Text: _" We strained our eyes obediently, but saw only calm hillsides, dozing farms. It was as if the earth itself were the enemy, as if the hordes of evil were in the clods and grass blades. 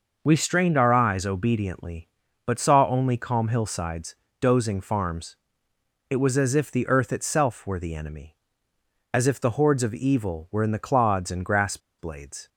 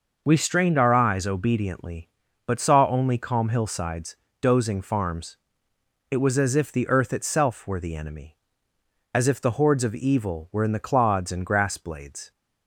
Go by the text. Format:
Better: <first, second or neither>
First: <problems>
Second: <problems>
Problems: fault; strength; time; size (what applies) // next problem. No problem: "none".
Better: second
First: pauses between "grass" and "blades"; slight; at 11.7 s; 0.20 s long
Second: none